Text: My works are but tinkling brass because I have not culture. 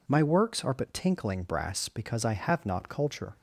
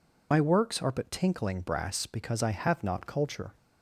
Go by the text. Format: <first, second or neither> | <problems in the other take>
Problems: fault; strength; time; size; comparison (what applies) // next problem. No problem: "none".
first | loses the start of "My"; at 0.3 s; 50 ms